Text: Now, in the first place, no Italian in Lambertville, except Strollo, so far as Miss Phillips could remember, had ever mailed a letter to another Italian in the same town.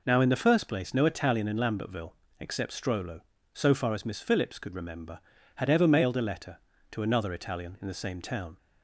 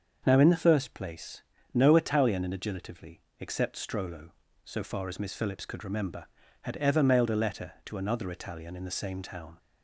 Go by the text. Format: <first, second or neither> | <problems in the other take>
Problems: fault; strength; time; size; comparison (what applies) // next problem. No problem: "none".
first | starts louder than the rest; until 1.2 s; 6.5 dB // says "Agilitively" for "Lambertville"; at 2.5 s